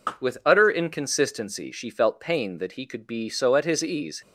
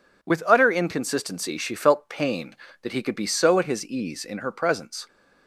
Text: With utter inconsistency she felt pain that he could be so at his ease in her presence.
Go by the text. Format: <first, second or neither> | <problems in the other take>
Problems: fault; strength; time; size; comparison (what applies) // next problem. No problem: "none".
second | stops before "in her presence"; at 4.2 s